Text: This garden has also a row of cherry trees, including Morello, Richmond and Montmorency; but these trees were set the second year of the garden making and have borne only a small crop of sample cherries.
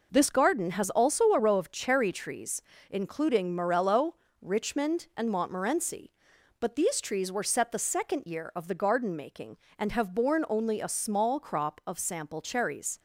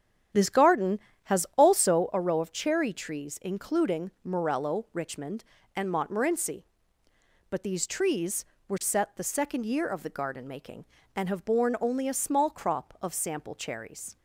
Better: first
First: none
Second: starts louder than the rest; strong; until 2.1 s; 9.5 dB

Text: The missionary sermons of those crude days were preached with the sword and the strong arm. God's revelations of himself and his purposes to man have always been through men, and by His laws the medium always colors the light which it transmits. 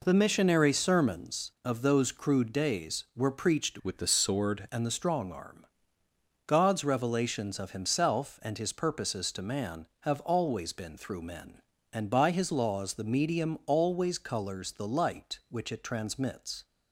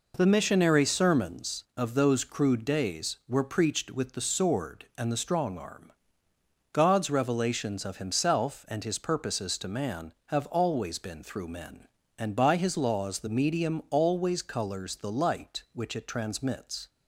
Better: second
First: changes voice from "with" to "sword"; from 3.8 to 4.6 s; 0.8 s long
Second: none

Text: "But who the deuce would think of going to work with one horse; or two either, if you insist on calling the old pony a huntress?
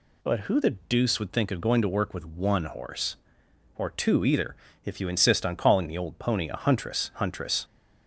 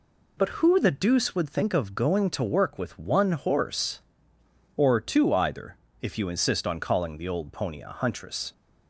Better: second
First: says "huntress" twice; at 7.1 s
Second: none

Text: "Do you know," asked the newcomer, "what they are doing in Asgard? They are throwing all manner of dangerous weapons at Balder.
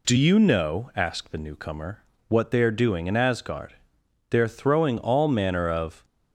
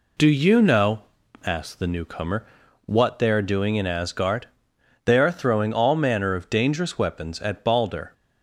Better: second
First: stops before "dangerous weapons at Balder"; at 6.0 s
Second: none

